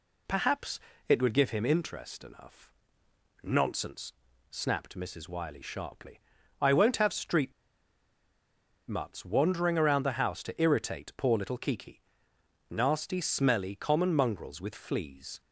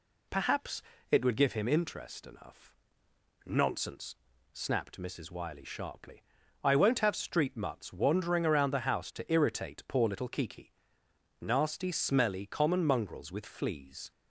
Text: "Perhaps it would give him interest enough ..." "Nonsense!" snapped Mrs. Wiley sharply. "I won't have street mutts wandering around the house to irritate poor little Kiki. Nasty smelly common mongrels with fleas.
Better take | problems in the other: second | pauses between "Perhaps" and "it"; slight; at 0.7 s; 0.30 s long; slight in the second // pauses between "street" and "mutts"; strong; at 7.5 s; 1.3 s long

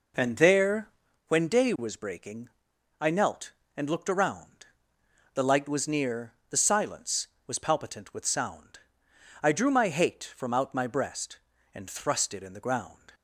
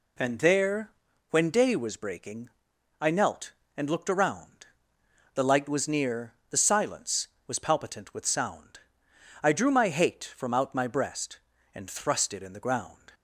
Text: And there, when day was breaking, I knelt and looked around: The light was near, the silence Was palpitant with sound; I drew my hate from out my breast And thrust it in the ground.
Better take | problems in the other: second | starts louder than the rest; noticeable; until 1.2 s; 4.5 dB

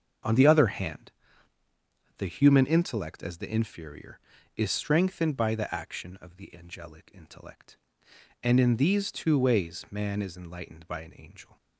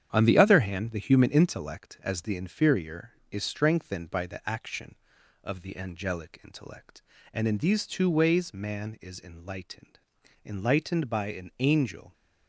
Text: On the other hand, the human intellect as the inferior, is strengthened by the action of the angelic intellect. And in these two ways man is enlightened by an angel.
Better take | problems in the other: first | starts louder than the rest; strong; until 1.1 s; 9 dB; also in the first // says "enlightened" twice; at 10.4 s

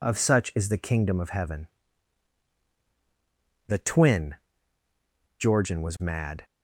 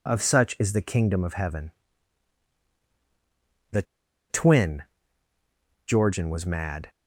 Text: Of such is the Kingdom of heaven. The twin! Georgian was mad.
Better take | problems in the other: first | pauses between "The" and "twin"; noticeable; at 3.8 s; 0.46 s long

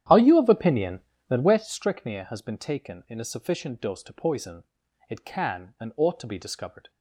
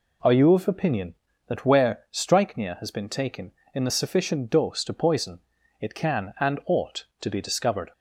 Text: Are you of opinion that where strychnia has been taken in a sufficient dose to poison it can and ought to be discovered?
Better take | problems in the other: second | starts louder than the rest; strong; until 1.8 s; 10.5 dB // pauses between "poison" and "it"; noticeable; at 4.6 s; 0.48 s long; also in the second

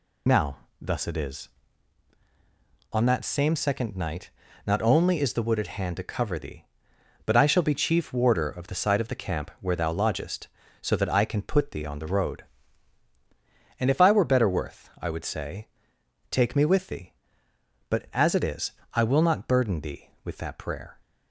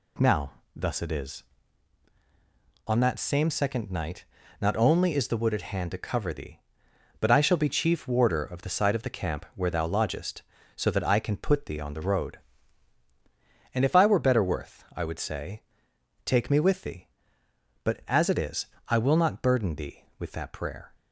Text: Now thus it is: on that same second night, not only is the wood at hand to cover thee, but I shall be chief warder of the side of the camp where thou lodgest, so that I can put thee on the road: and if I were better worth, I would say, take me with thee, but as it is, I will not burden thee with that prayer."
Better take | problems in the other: second | loses the start of "Now"; at 0.2 s; 50 ms // pauses between "Now" and "thus"; slight; at 0.5 s; 0.24 s long; slight in the second

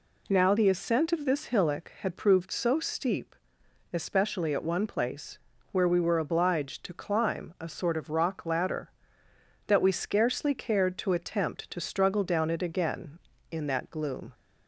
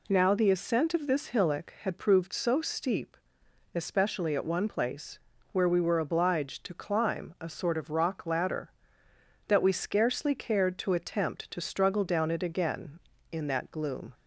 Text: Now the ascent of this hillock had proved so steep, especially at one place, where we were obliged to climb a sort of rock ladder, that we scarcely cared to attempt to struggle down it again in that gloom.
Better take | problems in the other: neither | none

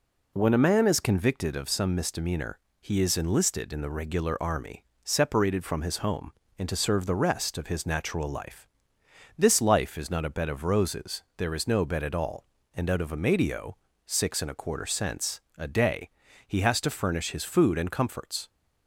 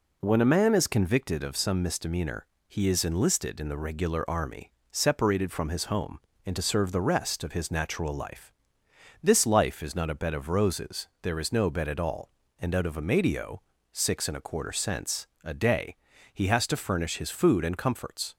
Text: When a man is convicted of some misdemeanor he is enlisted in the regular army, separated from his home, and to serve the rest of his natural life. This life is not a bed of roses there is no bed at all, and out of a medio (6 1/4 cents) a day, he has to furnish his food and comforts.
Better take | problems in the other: neither | pauses between "misdemeanor" and "he"; slight; the same in both

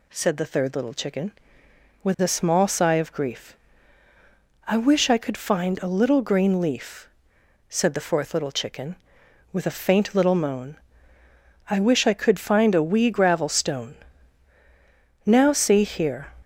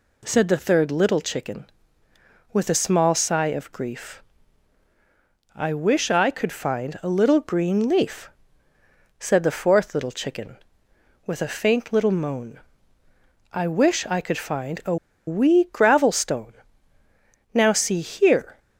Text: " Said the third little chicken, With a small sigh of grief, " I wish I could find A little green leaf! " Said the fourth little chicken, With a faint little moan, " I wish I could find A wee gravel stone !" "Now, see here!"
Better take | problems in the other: first | pauses between "A" and "wee"; slight; at 14.9 s; 0.31 s long

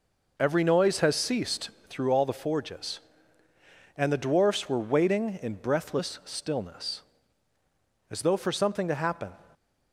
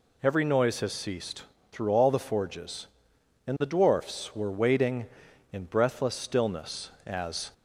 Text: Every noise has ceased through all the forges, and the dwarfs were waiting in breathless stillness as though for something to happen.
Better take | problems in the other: first | pauses between "ceased" and "through"; slight; at 1.4 s; 0.28 s long; slight in the first // stops before "though for something to happen"; at 7.5 s

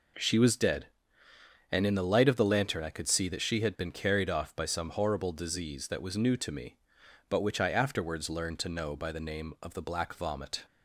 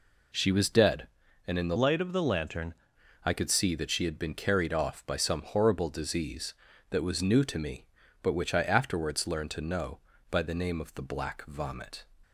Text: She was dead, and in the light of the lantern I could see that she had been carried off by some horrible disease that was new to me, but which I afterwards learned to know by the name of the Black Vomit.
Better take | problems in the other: first | changes voice from "light" to "lantern"; from 1.7 to 2.7 s; 1.0 s long

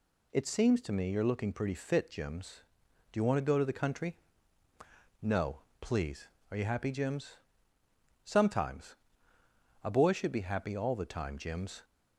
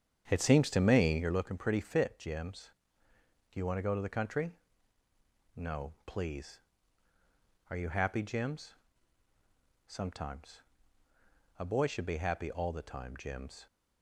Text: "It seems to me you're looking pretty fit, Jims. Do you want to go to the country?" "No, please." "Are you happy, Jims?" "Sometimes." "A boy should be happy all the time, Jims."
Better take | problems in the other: first | starts louder than the rest; strong; until 1.4 s; 8 dB

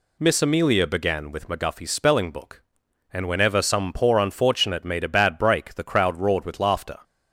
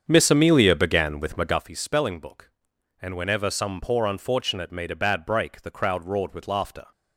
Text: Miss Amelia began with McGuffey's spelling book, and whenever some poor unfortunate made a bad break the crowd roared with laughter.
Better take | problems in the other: first | starts louder than the rest; strong; until 1.7 s; 7.5 dB

